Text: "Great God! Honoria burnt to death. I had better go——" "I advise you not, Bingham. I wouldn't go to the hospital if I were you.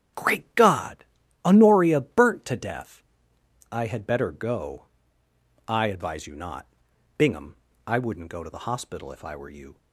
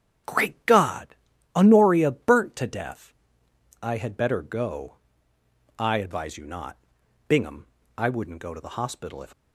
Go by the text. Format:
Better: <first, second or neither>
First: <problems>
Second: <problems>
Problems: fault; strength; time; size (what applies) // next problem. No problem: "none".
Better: first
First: starts louder than the rest; strong; until 1.5 s; 9.5 dB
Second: starts louder than the rest; strong; until 1.6 s; 9 dB // stops before "I were you"; at 9.3 s